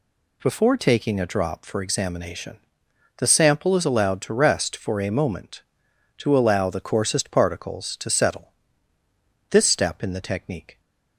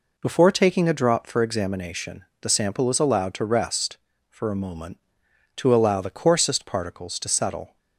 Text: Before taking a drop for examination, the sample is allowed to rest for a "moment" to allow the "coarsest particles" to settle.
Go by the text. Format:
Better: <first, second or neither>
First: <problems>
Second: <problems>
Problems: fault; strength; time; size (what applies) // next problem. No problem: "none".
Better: second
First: goes on to say "This step in the technique"; noticeable; from 9.4 s on; 1.3 s long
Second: none